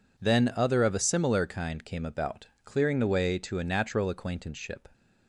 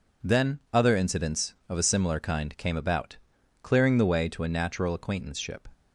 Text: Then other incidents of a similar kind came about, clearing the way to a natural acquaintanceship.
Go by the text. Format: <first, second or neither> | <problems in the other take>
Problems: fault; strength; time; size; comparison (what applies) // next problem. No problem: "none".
second | skips "incidents"; at 0.8 s